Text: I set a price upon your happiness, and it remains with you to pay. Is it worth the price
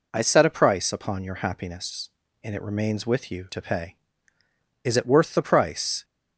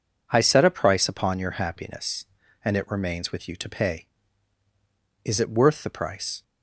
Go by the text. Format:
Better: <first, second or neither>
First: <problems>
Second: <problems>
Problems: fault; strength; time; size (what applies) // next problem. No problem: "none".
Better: neither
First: none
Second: none